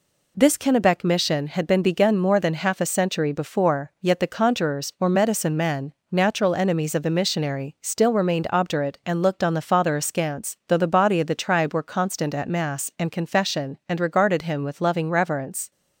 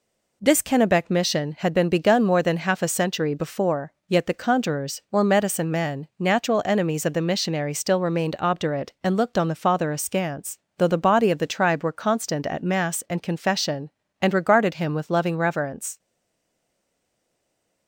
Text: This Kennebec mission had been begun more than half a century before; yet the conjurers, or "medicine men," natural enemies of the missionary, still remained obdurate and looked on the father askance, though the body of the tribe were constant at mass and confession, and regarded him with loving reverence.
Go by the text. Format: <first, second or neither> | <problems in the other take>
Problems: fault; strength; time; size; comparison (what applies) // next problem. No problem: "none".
first | stays silent after the last word; noticeable; from 15.9 s on; 1.9 s long